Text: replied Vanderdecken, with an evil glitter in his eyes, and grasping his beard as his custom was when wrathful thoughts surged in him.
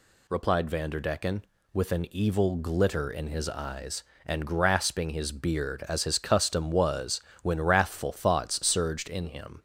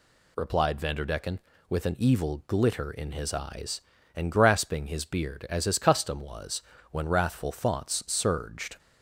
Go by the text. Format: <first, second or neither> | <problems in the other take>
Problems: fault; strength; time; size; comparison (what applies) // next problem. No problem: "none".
first | pauses between "was" and "when"; slight; at 6.6 s; 0.30 s long; slight in the first // stops before "in him"; at 8.7 s